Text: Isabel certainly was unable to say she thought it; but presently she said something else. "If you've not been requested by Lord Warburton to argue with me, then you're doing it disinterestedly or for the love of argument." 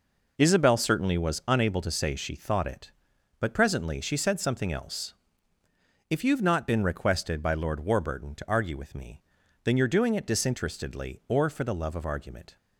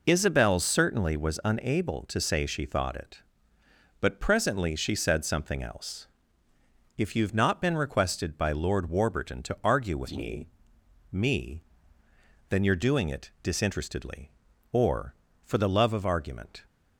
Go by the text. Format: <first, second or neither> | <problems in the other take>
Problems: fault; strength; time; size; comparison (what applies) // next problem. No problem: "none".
first | says "me" twice; at 11.0 s